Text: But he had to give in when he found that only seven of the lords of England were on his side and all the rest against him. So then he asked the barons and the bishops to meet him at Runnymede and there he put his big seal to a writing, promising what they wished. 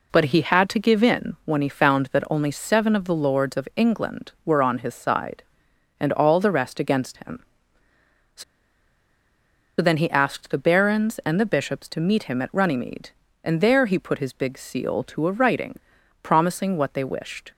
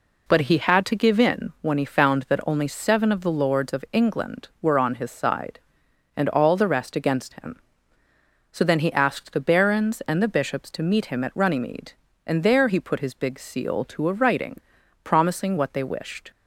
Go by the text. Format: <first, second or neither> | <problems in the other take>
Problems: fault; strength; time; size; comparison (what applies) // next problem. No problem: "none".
second | pauses between "So" and "then"; strong; at 8.4 s; 1.3 s long